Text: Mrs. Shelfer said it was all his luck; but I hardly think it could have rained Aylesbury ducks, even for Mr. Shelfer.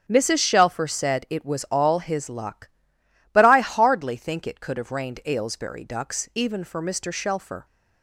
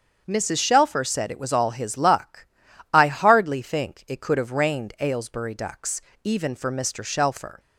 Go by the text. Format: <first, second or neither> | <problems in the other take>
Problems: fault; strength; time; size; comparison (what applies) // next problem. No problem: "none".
first | starts louder than the rest; until 1.2 s; 7 dB; also in the first // skips "but"; at 2.7 s